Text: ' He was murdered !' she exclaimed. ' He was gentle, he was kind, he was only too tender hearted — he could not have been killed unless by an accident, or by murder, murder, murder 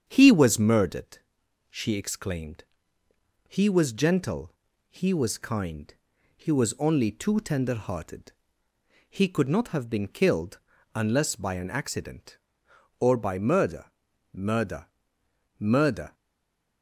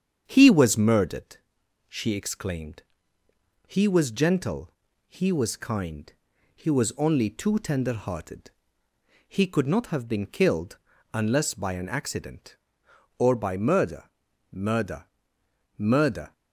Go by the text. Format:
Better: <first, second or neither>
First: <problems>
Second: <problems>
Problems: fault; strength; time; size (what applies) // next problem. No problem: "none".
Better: second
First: starts louder than the rest; strong; until 1.0 s; 7.5 dB // pauses between "killed" and "unless"; slight; at 10.5 s; 0.36 s long // stays silent after the last word; slight; from 16.1 s on; 0.7 s long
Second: starts louder than the rest; strong; until 1.2 s; 7.5 dB // pauses between "killed" and "unless"; slight; at 10.7 s; 0.36 s long